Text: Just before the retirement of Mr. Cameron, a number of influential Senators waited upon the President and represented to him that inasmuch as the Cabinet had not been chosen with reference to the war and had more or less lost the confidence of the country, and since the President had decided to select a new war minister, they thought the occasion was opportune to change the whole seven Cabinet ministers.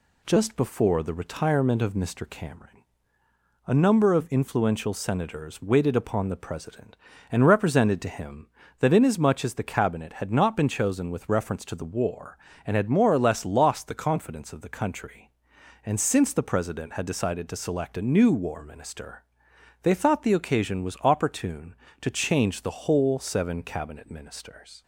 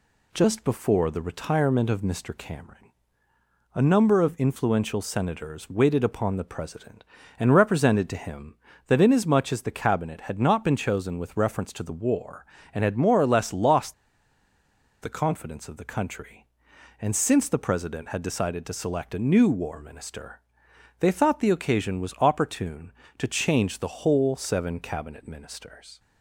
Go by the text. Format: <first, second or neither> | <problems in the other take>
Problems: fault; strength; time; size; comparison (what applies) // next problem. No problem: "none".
first | pauses between "lost" and "the"; at 13.9 s; 1.0 s long